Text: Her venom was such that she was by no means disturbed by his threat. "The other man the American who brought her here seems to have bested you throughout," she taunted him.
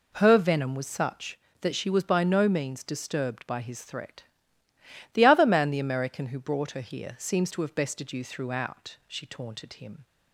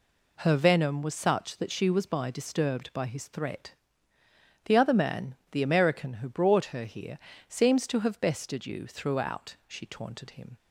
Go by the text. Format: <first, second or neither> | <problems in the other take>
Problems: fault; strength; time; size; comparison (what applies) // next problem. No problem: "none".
first | skips "no means"; at 2.2 s // pauses between "man" and "the"; slight; at 5.3 s; 0.18 s long // pauses between "here" and "seems"; slight; at 7.1 s; 0.32 s long